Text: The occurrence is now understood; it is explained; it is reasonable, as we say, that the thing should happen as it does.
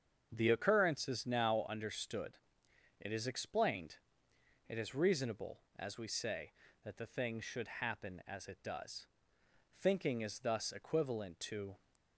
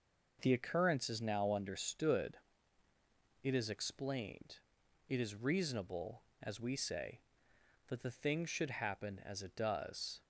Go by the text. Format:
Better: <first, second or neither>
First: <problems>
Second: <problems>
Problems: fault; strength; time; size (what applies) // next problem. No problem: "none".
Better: second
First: starts louder than the rest; strong; until 1.3 s; 7 dB // goes on to say "Thinking is thus equivalent to"; strong; from 9.7 s on; 1.9 s long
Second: none